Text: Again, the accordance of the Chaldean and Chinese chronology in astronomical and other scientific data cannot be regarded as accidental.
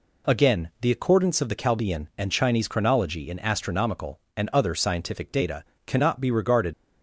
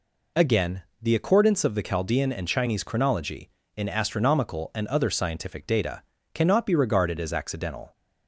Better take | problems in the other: second | pauses between "data" and "cannot"; slight; at 5.6 s; 0.22 s long; slight in the second // stops before "as accidental"; at 6.7 s

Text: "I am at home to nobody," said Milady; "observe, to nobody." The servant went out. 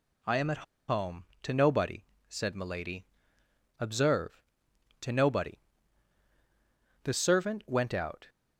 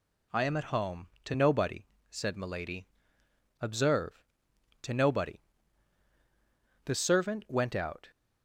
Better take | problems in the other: second | pauses between "at" and "home"; slight; at 0.6 s; 0.26 s long

